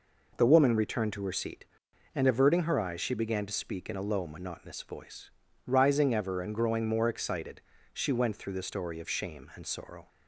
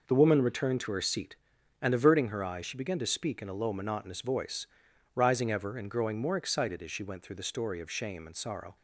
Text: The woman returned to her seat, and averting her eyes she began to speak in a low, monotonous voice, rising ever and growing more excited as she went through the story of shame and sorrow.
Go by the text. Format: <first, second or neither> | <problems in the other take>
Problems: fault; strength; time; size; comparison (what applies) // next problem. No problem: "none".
second | skips "as"; at 7.7 s